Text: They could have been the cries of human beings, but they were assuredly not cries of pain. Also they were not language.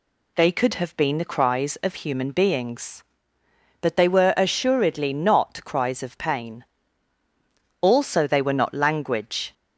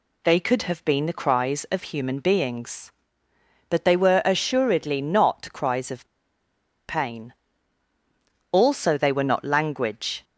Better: first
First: none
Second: pauses between "of" and "pain"; noticeable; at 6.0 s; 0.81 s long

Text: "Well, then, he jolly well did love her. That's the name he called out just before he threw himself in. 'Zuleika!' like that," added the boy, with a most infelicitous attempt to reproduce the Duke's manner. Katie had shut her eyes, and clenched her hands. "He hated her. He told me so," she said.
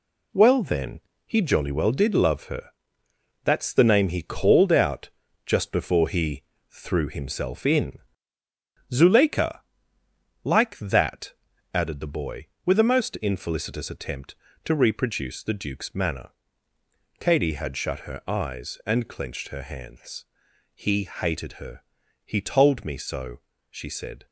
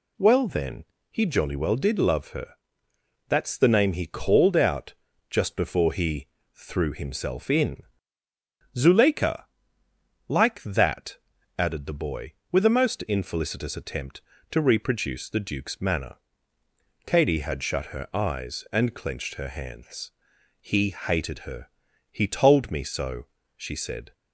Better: second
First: gets quieter; throughout; 7 dB // pauses between "out" and "just"; at 5.0 s; 0.38 s long // pauses between "he" and "threw"; slight; at 6.4 s; 0.28 s long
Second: pauses between "out" and "just"; at 4.9 s; 0.38 s long // pauses between "he" and "threw"; slight; at 6.2 s; 0.28 s long

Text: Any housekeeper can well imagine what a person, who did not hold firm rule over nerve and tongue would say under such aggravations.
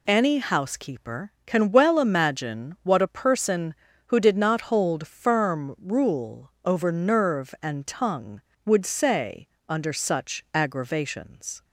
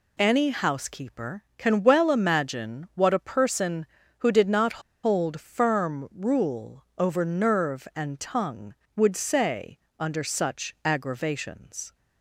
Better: first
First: pauses between "say" and "under"; slight; at 9.4 s; 0.20 s long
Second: pauses between "not" and "hold"; slight; at 4.7 s; 0.24 s long // pauses between "say" and "under"; slight; at 9.7 s; 0.20 s long

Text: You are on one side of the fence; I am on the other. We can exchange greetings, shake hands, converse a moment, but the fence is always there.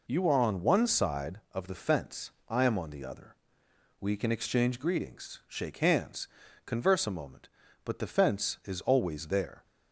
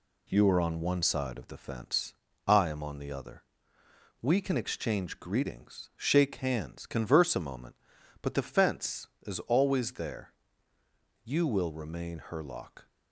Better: first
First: none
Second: goes on to say "You will remain Herlock"; from 11.2 s on; 1.6 s long

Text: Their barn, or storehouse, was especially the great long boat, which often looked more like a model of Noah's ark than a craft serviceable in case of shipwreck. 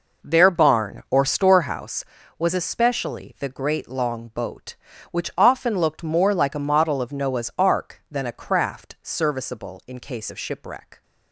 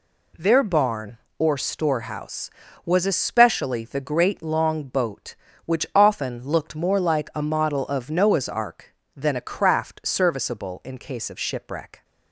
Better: second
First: starts louder than the rest; noticeable; until 2.0 s; 5 dB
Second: none

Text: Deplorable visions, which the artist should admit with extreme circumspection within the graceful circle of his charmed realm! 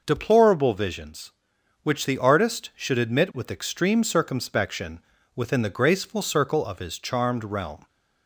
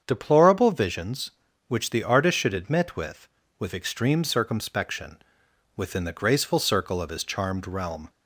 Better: first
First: pauses between "circumspection" and "within"; slight; at 4.9 s; 0.36 s long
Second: starts louder than the rest; strong; until 1.0 s; 7.5 dB // says "with" twice; at 3.5 s // pauses between "circumspection" and "within"; noticeable; at 5.1 s; 0.60 s long

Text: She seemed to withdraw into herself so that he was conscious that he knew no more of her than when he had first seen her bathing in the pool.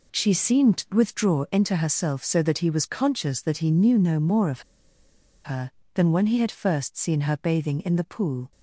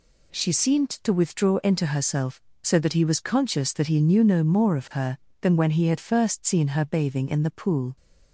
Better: second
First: pauses between "of" and "her"; noticeable; at 4.6 s; 0.83 s long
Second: none

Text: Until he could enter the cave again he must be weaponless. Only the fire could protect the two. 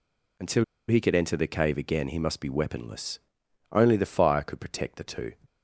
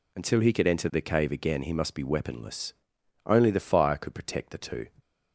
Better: second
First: pauses between "Until" and "he"; slight; at 0.6 s; 0.24 s long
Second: none

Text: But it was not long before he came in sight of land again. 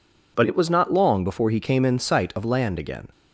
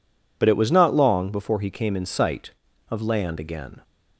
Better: neither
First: none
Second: none

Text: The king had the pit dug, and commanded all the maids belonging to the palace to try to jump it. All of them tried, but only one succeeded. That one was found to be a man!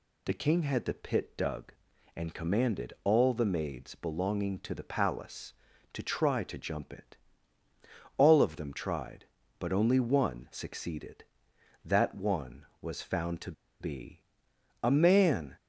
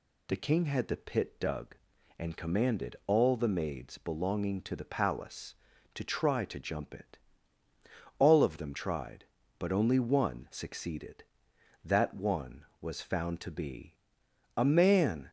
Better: second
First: pauses between "to" and "be"; slight; at 13.5 s; 0.28 s long // pauses between "be" and "a"; noticeable; at 14.2 s; 0.62 s long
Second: pauses between "be" and "a"; noticeable; at 13.9 s; 0.62 s long

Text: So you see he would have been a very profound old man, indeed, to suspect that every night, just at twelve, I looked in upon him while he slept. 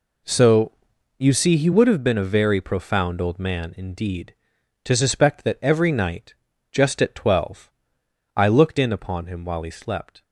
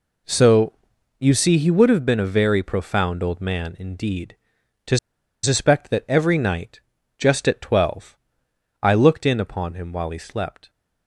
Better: first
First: pauses between "So" and "you"; noticeable; at 0.7 s; 0.46 s long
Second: pauses between "So" and "you"; noticeable; at 0.7 s; 0.46 s long // pauses between "to" and "suspect"; noticeable; at 4.9 s; 0.46 s long

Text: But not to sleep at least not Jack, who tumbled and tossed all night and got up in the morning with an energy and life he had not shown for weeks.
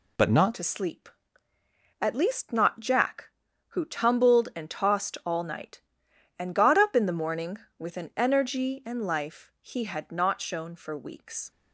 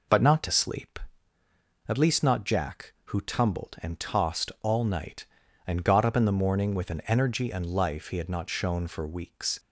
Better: second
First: changes voice at "to"; from 0.5 s on; 11.0 s long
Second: none

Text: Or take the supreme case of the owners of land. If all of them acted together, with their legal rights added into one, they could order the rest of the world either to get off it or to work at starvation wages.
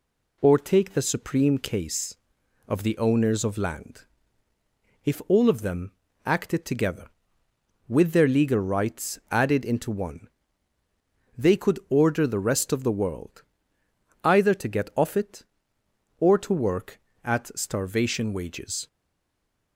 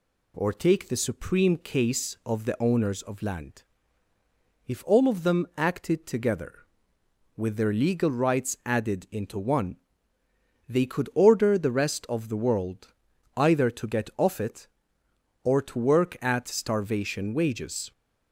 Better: second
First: pauses between "them" and "acted"; slight; at 5.9 s; 0.34 s long // pauses between "world" and "either"; noticeable; at 13.4 s; 0.80 s long // stays silent after the last word; slight; from 18.8 s on; 0.9 s long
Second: pauses between "world" and "either"; at 12.9 s; 0.42 s long

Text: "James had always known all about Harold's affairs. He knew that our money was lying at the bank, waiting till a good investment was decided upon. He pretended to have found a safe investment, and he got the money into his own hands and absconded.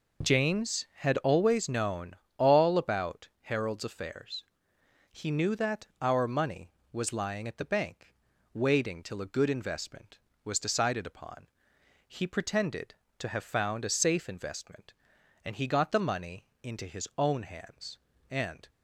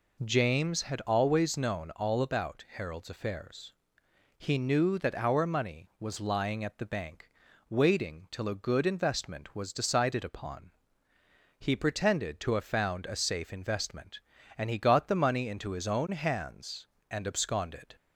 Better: second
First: pauses between "known" and "all"; slight; at 2.1 s; 0.22 s long // pauses between "money" and "into"; slight; at 16.4 s; 0.16 s long // stops before "absconded"; at 18.6 s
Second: none

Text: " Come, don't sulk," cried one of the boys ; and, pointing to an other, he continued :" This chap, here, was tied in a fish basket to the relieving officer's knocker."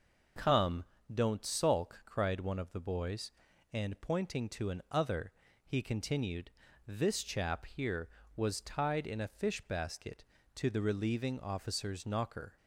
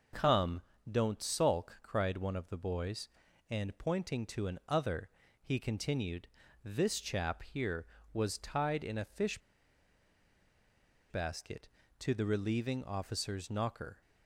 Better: first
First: none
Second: pauses between "fish" and "basket"; strong; at 9.3 s; 1.7 s long

